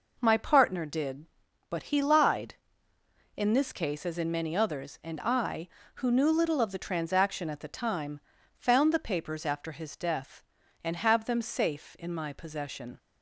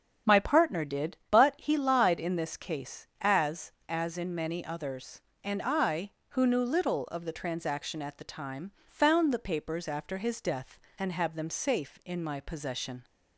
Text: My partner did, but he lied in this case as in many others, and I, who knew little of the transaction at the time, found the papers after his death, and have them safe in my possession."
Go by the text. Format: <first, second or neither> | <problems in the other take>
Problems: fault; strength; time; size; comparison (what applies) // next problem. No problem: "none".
first | starts louder than the rest; until 1.3 s; 7 dB // says "as" twice; at 3.9 s